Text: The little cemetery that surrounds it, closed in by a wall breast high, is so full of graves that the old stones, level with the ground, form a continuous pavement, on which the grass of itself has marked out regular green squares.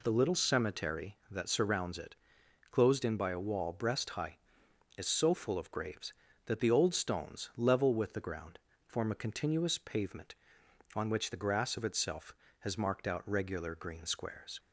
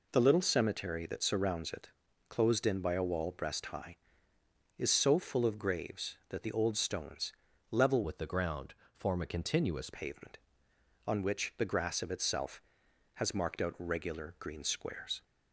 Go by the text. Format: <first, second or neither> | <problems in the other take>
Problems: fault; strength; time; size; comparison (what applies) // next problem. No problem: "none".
first | changes voice from "with" to "continuous"; from 8.0 to 9.8 s; 1.8 s long